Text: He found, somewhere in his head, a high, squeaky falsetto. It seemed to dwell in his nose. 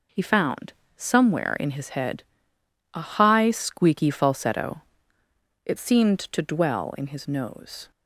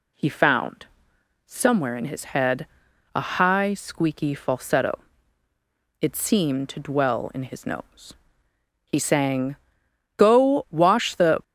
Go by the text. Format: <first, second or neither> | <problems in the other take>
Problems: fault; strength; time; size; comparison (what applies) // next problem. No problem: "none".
first | goes on to say "He sang Go wash the"; strong; from 8.8 s on; 2.5 s long